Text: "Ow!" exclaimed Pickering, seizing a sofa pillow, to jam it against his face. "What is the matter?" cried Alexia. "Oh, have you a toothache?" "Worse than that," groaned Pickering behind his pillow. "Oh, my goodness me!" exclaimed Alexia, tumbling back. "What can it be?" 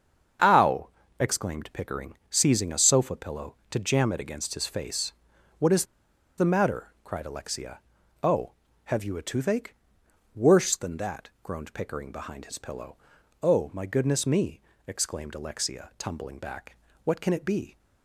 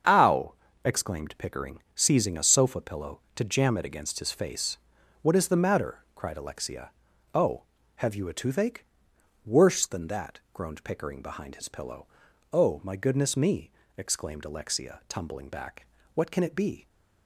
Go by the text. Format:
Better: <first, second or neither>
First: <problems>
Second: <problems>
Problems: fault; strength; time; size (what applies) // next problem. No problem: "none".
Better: second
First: starts louder than the rest; strong; until 1.7 s; 7 dB // pauses between "is" and "the"; noticeable; at 5.8 s; 0.53 s long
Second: starts louder than the rest; strong; until 1.4 s; 7 dB